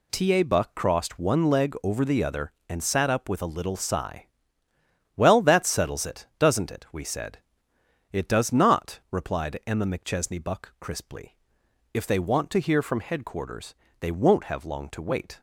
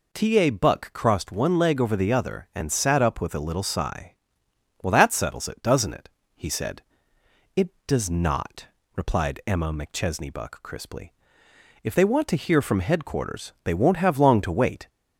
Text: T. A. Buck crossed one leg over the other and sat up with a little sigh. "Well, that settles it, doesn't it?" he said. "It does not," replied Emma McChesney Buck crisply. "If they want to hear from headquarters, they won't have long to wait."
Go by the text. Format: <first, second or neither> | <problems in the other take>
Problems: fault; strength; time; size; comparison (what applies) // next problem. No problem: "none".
second | says "we" for "he"; at 6.9 s